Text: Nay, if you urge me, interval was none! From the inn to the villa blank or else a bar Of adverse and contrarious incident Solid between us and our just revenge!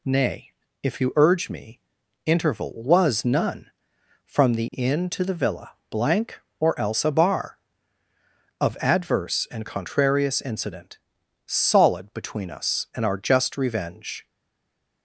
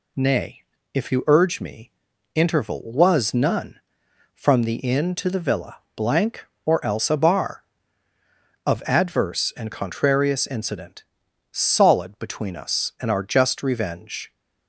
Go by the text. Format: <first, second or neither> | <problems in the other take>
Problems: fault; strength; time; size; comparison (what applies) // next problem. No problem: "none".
second | pauses between "villa" and "blank"; slight; at 5.7 s; 0.18 s long; slight in the second // pauses between "incident" and "Solid"; noticeable; at 10.9 s; 0.50 s long; noticeable in the second // stays silent after the last word; slight; from 14.2 s on; 0.8 s long